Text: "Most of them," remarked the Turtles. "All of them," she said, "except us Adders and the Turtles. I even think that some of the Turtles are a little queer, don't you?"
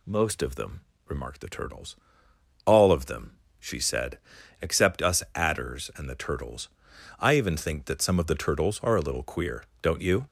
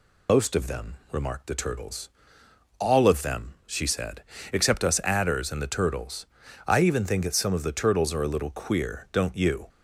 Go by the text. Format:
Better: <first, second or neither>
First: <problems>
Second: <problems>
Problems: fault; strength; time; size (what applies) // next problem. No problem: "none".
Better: first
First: none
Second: loses the start of "Most"; at 0.2 s; 95 ms